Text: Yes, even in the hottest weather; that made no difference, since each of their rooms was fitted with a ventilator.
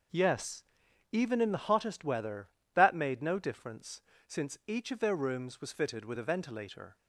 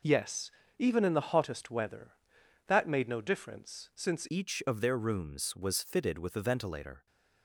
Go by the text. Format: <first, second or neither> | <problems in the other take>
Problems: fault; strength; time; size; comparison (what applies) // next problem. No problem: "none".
first | changes voice at "each"; from 4.2 s on; 2.8 s long